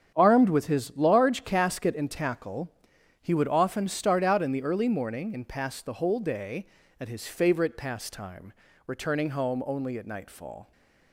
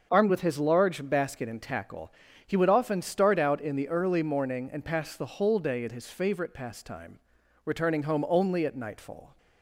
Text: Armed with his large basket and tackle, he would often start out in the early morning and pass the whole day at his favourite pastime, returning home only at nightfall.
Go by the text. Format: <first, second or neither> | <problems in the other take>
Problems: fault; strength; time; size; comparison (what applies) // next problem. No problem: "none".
second | starts louder than the rest; strong; until 1.1 s; 8 dB; also in the second // says "casket" for "basket"; at 1.4 s